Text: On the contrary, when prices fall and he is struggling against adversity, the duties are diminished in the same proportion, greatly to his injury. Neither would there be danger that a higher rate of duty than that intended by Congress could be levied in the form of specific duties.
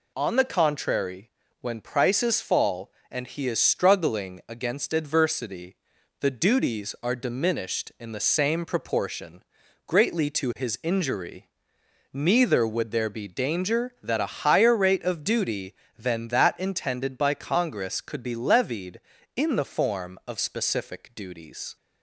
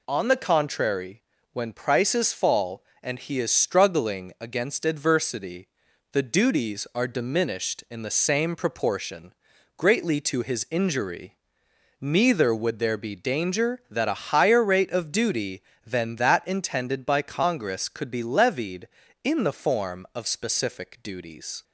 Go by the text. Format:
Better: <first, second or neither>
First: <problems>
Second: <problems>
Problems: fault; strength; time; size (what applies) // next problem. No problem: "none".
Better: neither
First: none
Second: none